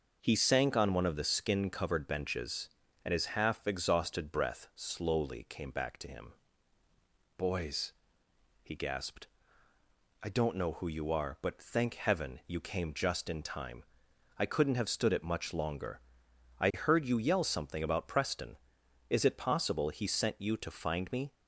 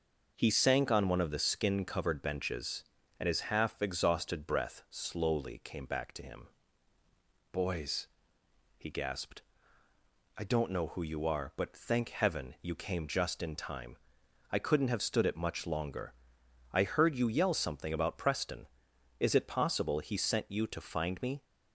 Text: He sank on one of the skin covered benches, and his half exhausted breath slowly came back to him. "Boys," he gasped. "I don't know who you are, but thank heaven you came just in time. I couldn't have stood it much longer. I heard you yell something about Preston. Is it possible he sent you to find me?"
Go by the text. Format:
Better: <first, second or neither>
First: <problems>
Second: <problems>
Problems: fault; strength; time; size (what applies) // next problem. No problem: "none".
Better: neither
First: none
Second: none